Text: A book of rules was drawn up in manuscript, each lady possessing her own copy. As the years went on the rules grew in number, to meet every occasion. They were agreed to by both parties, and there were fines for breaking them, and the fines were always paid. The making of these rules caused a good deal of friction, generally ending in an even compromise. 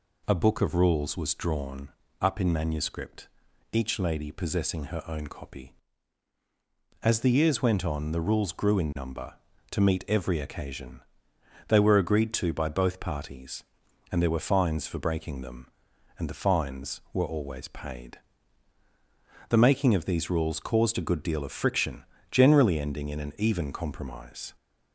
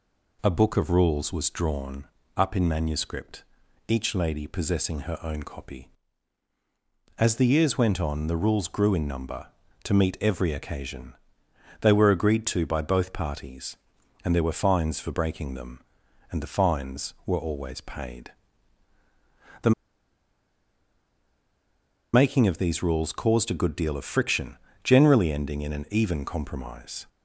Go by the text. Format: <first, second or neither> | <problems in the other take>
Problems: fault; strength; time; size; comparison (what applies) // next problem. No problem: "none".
first | pauses between "drawn" and "up"; slight; at 2.0 s; 0.28 s long; slight in the first // pauses between "The" and "making"; strong; at 19.7 s; 2.4 s long